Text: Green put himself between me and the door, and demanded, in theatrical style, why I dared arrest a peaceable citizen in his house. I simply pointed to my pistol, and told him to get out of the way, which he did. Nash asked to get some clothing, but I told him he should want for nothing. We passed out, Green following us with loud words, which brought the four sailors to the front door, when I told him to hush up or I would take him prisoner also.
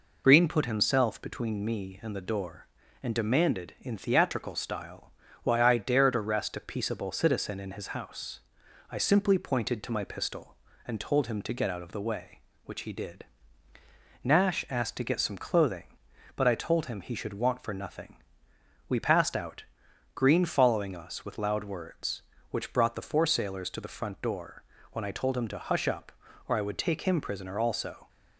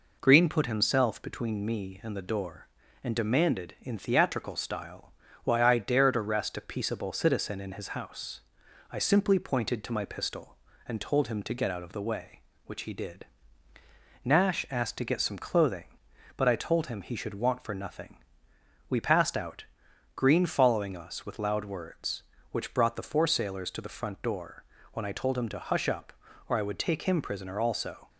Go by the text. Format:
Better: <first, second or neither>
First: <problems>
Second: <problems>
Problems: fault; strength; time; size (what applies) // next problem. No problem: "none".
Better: second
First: loses the start of "Green"; at 0.2 s; 45 ms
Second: none